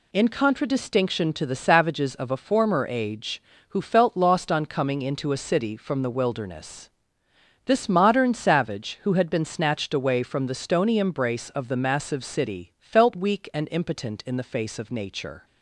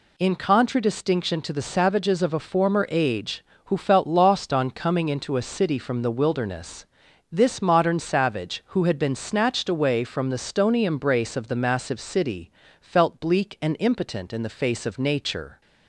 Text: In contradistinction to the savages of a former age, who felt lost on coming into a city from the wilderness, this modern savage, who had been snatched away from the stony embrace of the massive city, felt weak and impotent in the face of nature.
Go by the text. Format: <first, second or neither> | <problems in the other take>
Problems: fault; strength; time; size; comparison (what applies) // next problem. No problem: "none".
first | says "bleak" for "weak"; at 13.2 s